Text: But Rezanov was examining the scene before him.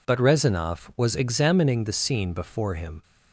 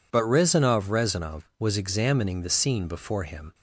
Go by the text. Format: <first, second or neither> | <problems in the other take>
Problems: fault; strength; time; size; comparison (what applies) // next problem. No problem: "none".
first | says "Rezanov" twice; at 0.8 s